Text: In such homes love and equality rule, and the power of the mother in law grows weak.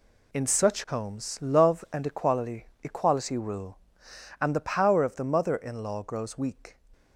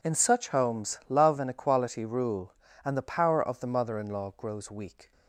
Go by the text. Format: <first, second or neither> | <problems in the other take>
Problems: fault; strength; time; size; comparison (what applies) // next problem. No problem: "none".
second | says "equality" twice; at 2.8 s